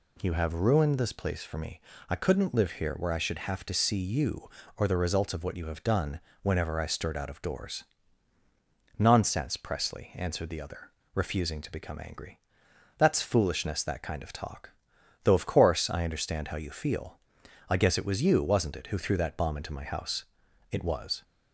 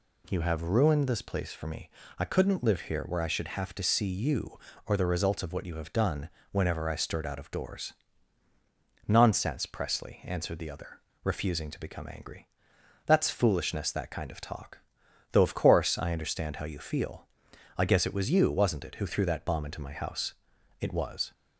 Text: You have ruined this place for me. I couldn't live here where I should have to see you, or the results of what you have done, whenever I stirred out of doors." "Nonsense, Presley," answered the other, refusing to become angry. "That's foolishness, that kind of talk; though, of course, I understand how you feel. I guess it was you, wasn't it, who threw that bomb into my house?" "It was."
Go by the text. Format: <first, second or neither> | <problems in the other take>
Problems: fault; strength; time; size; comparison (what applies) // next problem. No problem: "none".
neither | none